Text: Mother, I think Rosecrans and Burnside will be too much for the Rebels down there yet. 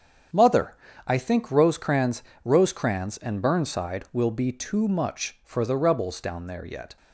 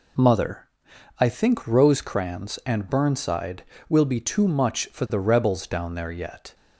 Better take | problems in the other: second | starts louder than the rest; strong; until 1.6 s; 8 dB // says "Rosecrans" twice; at 2.4 s

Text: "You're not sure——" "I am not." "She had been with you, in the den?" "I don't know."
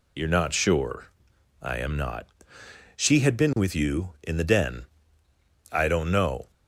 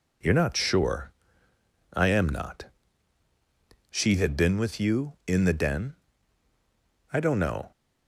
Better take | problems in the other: second | loses the start of "You're"; at 0.1 s; 50 ms

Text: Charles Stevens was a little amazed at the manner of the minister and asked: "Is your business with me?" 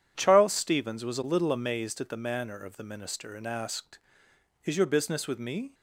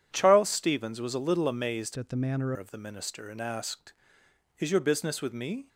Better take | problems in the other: first | changes voice from "at" to "manner"; from 1.9 to 2.5 s; 0.6 s long

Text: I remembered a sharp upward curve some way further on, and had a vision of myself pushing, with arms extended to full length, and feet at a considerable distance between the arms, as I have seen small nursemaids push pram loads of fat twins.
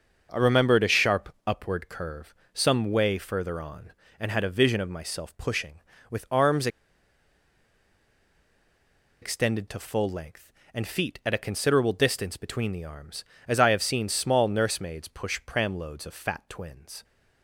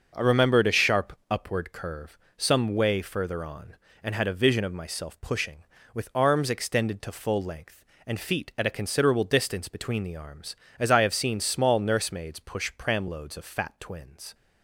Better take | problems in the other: second | starts louder than the rest; until 1.3 s; 6 dB; also in the second // pauses between "curve" and "some"; slight; at 2.3 s; 0.20 s long; slight in the second // pauses between "arms" and "extended"; strong; at 6.6 s; 2.5 s long

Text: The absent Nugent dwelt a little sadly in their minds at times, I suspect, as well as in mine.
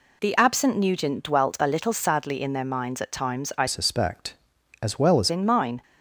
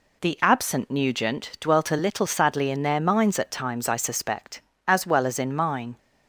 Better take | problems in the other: second | changes voice from "suspect" to "as"; from 3.6 to 5.2 s; 1.6 s long

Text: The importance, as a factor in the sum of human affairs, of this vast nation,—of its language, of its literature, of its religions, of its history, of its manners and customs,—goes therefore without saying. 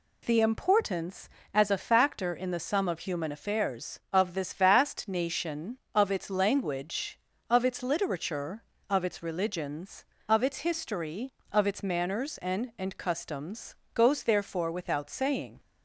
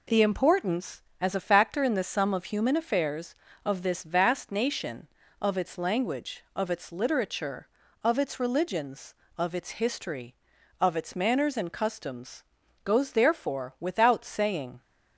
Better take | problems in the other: second | says "and" twice; at 12.7 s

